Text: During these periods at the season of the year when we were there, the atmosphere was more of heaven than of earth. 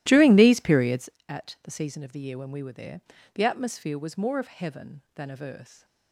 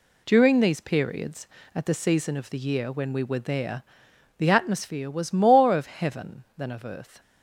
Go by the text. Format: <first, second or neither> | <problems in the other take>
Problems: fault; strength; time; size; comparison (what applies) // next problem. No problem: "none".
second | starts louder than the rest; strong; until 1.2 s; 15 dB